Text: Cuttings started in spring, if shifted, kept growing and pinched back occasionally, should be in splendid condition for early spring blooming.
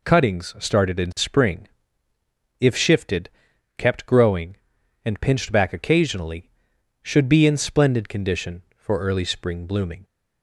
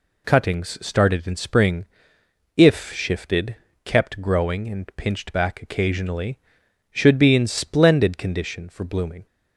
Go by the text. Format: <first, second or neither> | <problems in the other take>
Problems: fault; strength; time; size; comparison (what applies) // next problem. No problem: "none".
first | skips "early spring"; at 8.8 s